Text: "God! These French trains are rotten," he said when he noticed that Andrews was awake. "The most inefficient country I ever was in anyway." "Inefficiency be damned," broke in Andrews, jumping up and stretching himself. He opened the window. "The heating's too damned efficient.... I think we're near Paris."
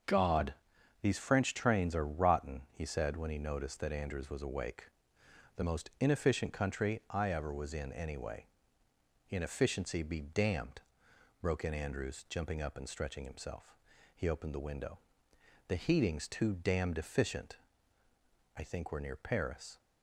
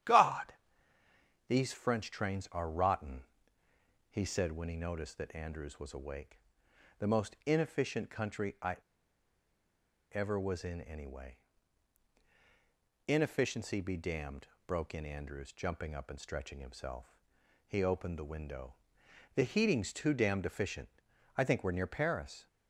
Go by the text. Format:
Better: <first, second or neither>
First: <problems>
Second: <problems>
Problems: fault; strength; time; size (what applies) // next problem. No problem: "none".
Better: first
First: starts louder than the rest; until 1.5 s; 7 dB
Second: starts louder than the rest; strong; until 1.9 s; 10.5 dB // pauses between "I" and "ever"; strong; at 8.7 s; 1.3 s long